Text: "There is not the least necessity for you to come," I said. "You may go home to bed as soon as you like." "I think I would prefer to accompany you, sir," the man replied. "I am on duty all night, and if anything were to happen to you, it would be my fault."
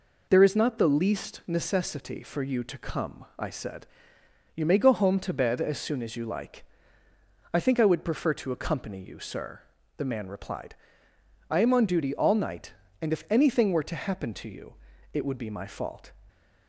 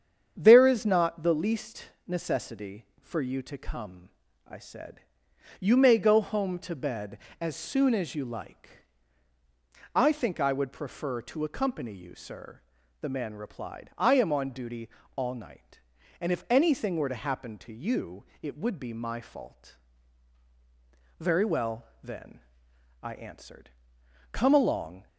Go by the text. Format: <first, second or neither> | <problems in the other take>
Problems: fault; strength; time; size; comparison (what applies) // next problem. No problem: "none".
first | starts louder than the rest; strong; until 1.3 s; 8 dB // pauses between "least" and "necessity"; slight; at 1.8 s; 0.18 s long // pauses between "duty" and "all"; slight; at 14.8 s; 0.26 s long // goes on to say "Very well then I answered come along"; strong; from 21.1 s on; 3.8 s long